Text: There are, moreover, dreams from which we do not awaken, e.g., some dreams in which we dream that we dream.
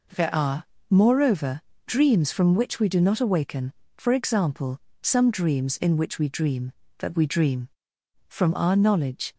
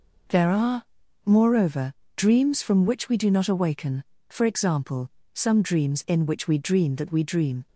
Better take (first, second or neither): second